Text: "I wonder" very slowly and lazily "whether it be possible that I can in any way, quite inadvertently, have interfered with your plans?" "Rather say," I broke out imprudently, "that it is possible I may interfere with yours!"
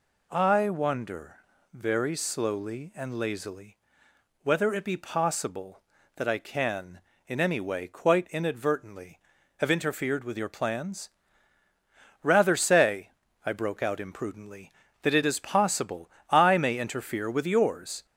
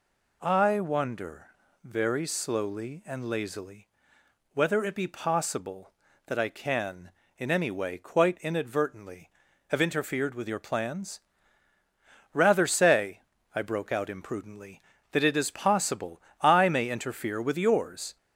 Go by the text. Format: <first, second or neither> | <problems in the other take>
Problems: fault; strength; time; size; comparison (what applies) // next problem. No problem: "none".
neither | pauses between "wonder" and "very"; slight; the same in both // pauses between "lazily" and "whether"; noticeable; the same in both // pauses between "possible" and "I"; slight; the same in both